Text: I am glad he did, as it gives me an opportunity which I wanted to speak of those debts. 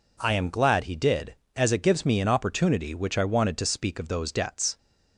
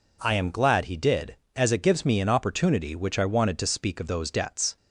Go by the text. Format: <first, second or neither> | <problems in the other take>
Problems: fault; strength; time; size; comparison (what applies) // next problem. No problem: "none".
neither | none